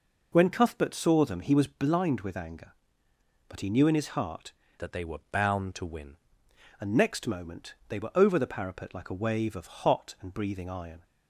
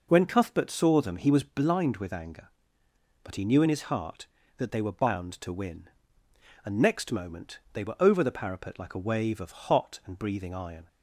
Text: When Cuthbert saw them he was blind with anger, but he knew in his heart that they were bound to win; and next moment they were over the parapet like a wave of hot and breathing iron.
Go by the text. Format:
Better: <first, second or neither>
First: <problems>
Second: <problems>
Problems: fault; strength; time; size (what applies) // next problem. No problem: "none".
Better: second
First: changes voice from "that" to "win"; from 4.7 to 6.1 s; 1.4 s long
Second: none